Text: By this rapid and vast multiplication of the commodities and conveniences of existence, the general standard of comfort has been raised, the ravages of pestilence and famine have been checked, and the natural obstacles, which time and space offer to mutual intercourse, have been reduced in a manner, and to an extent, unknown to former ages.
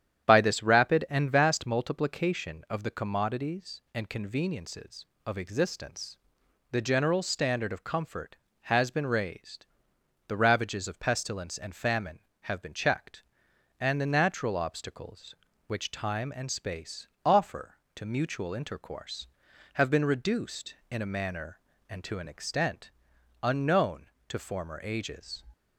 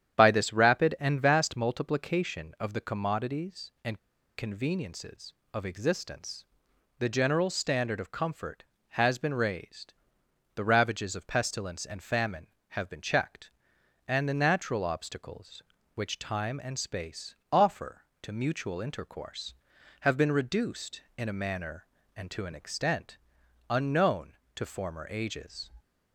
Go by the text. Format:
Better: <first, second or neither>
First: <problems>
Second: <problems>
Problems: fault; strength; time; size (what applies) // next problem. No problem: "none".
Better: first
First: starts louder than the rest; strong; until 1.3 s; 9.5 dB // pauses between "space" and "offer"; slight; at 17.0 s; 0.17 s long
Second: starts louder than the rest; strong; until 1.2 s; 9.5 dB // pauses between "and" and "conveniences"; at 3.9 s; 0.38 s long // pauses between "space" and "offer"; slight; at 17.3 s; 0.16 s long